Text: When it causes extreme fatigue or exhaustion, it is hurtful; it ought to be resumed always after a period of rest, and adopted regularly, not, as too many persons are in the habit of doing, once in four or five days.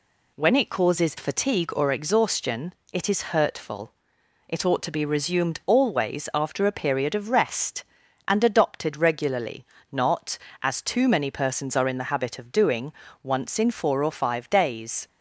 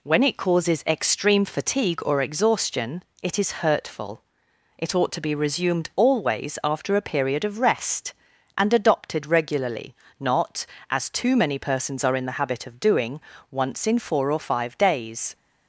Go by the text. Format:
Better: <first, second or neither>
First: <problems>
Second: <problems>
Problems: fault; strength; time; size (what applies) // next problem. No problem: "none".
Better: second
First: skips "extreme"; at 1.1 s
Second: none